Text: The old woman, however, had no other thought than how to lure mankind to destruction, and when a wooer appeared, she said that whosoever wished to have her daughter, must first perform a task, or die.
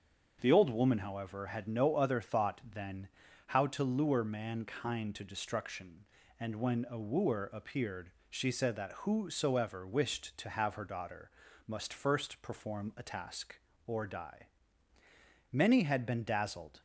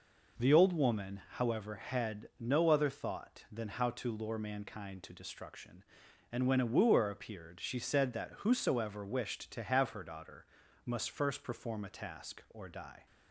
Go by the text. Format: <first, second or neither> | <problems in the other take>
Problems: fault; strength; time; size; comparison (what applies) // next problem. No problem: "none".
second | starts louder than the rest; until 1.4 s; 6.5 dB // pauses between "than" and "how"; at 3.0 s; 0.40 s long // goes on to say "Many had been dazzled"; noticeable; from 15.5 s on; 1.3 s long